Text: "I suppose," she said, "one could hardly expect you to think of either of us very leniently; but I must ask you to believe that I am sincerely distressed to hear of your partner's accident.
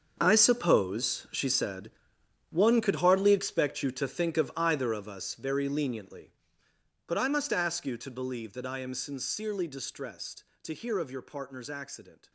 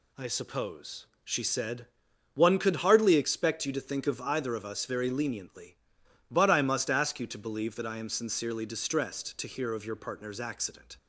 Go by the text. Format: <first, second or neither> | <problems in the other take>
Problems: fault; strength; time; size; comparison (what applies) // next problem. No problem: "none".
second | gets quieter; strong; throughout; 13.5 dB